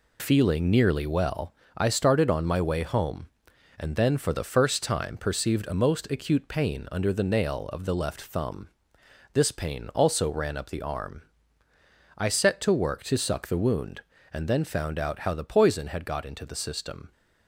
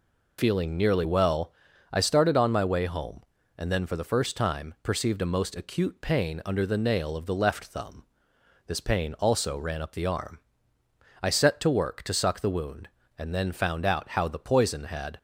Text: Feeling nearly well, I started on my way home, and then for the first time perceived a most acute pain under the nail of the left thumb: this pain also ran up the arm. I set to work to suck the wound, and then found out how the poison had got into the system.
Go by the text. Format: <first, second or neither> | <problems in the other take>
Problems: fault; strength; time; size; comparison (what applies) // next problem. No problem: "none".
first | stops before "got into the system"; at 15.1 s